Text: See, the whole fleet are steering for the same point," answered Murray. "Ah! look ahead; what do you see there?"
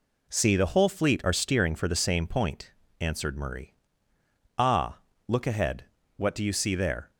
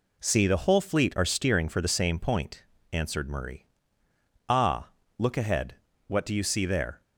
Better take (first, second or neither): neither